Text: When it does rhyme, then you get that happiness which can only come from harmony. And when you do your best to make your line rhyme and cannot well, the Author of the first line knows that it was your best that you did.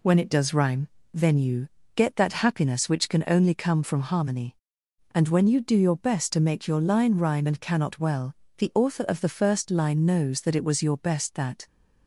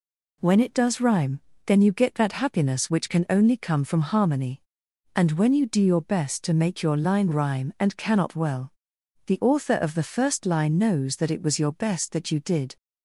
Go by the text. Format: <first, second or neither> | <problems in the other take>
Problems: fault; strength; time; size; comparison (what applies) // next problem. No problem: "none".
second | pauses between "you" and "get"; slight; at 1.6 s; 0.26 s long // stops before "you did"; at 11.6 s